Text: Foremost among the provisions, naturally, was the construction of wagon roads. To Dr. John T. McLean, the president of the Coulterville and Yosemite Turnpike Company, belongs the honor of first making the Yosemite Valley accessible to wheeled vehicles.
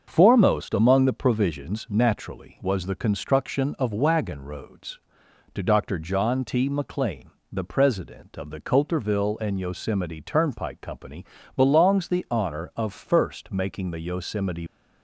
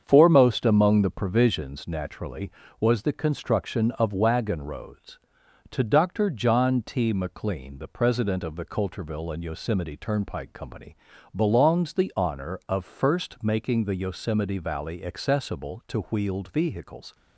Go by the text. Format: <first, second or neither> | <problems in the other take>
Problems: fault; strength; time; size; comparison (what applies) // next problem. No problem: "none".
second | starts louder than the rest; until 1.0 s; 6.5 dB; strong in the second // stops before "Valley accessible to wheeled vehicles"; at 14.6 s